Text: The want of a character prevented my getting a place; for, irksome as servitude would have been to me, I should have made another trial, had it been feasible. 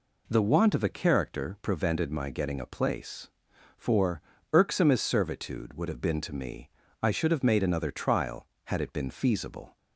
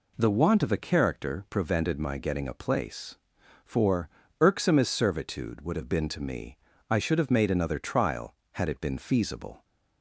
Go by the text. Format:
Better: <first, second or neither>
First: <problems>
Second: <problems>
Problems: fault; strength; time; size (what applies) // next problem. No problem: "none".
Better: neither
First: none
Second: none